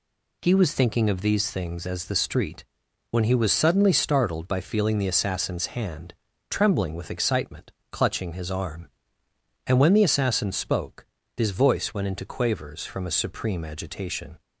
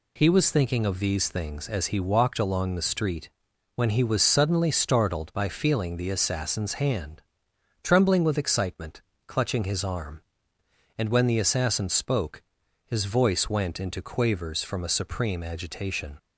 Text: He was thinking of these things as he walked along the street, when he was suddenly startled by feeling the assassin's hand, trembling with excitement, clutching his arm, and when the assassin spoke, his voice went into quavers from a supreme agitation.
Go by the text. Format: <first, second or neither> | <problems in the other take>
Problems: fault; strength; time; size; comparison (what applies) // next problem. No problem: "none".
second | skips "he walked along"; at 2.0 s